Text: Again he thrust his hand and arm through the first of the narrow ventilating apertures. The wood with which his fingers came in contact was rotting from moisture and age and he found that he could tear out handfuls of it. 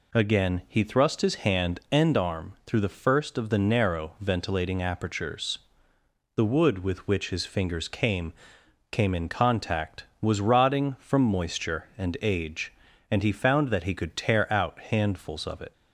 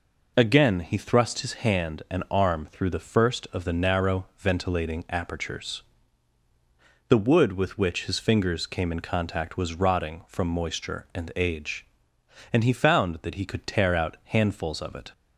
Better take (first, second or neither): second